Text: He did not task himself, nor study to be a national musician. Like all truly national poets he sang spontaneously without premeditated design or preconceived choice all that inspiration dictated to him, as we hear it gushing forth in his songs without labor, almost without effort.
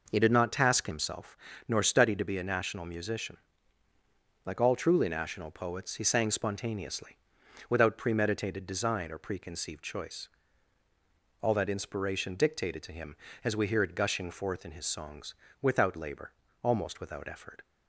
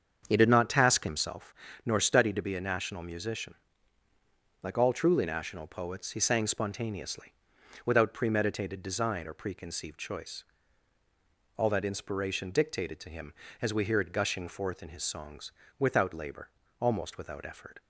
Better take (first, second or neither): first